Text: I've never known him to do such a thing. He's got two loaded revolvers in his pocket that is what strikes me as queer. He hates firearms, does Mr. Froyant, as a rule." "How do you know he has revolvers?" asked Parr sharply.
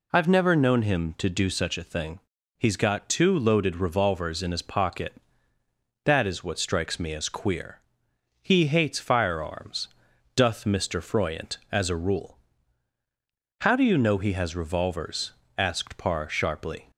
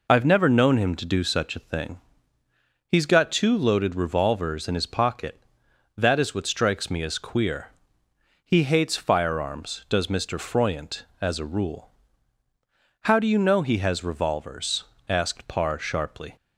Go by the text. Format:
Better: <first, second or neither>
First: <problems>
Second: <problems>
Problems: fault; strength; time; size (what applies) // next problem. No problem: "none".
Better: second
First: says "doth" for "does"; at 10.3 s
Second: none